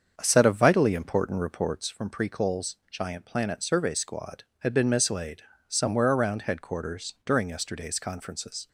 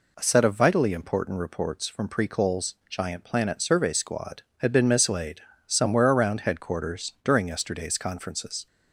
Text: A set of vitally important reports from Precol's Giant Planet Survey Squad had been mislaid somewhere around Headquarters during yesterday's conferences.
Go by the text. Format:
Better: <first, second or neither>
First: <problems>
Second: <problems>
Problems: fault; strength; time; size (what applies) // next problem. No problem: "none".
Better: second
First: starts louder than the rest; strong; until 2.0 s; 7 dB // pauses between "mislaid" and "somewhere"; slight; at 5.4 s; 0.26 s long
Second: pauses between "mislaid" and "somewhere"; slight; at 5.4 s; 0.26 s long